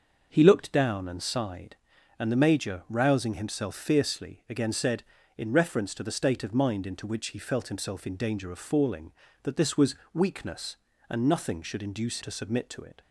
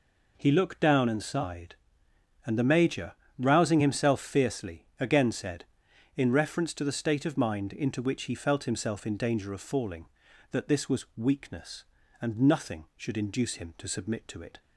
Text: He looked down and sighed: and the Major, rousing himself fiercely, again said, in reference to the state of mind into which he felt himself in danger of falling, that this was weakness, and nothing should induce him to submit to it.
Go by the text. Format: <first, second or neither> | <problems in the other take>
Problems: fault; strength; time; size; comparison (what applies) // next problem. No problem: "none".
second | starts louder than the rest; until 1.3 s; 6.5 dB // pauses between "was" and "weakness"; slight; at 9.9 s; 0.18 s long // skips "him"; at 12.2 s